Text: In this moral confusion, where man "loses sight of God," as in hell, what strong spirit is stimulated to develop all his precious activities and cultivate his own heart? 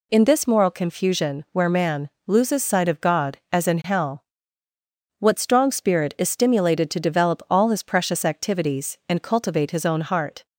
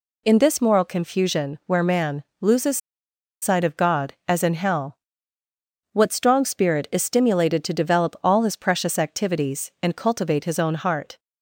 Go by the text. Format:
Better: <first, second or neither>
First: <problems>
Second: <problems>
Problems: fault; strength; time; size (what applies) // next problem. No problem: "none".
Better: first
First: pauses between "man" and "loses"; slight; at 2.0 s; 0.18 s long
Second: pauses between "man" and "loses"; slight; at 2.2 s; 0.18 s long // pauses between "loses" and "sight"; noticeable; at 2.7 s; 0.64 s long